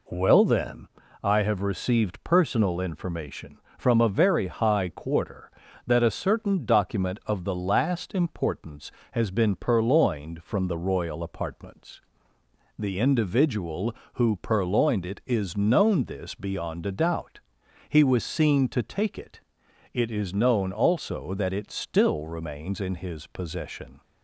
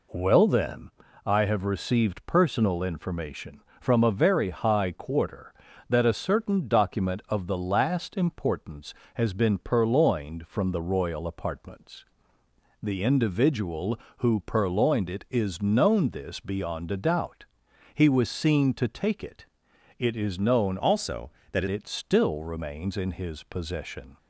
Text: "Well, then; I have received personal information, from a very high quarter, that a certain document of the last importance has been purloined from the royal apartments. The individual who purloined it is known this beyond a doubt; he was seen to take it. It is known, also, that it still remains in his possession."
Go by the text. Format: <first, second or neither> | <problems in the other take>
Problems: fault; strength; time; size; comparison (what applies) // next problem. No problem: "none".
first | changes voice from "also" to "that"; from 20.7 to 21.6 s; 0.9 s long